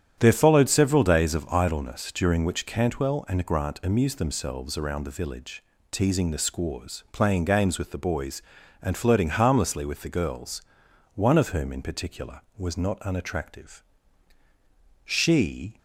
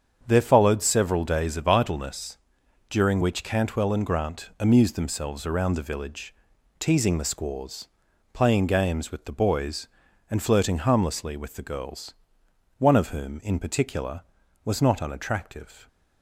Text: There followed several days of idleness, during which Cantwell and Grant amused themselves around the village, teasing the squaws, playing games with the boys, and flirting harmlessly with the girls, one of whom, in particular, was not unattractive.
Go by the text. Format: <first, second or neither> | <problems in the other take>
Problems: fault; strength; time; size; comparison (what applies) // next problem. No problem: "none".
second | starts louder than the rest; strong; until 1.2 s; 9 dB; strong in the second // goes on to say "She"; noticeable; from 15.0 s on; 0.74 s long